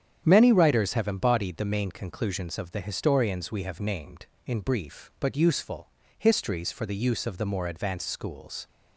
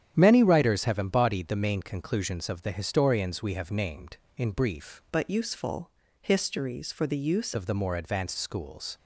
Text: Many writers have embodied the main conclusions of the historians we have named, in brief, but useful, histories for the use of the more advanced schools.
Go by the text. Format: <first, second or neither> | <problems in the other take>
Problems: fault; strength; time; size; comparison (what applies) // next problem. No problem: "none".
first | starts louder than the rest; strong; until 1.1 s; 9.5 dB; strong in the first // changes voice from "but" to "use"; from 5.1 to 7.5 s; 2.4 s long